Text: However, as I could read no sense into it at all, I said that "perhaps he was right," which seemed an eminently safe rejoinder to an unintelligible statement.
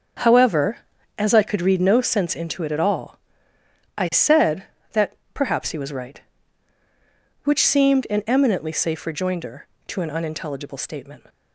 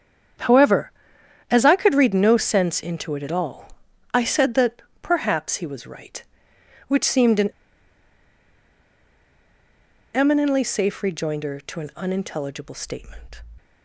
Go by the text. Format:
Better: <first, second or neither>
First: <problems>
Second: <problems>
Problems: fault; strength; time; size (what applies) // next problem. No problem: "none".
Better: first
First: starts louder than the rest; until 1.6 s; 6.5 dB // pauses between "that" and "perhaps"; slight; at 5.1 s; 0.18 s long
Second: starts louder than the rest; strong; until 2.0 s; 8 dB // pauses between "that" and "perhaps"; slight; at 4.8 s; 0.20 s long // pauses between "an" and "eminently"; strong; at 7.5 s; 2.6 s long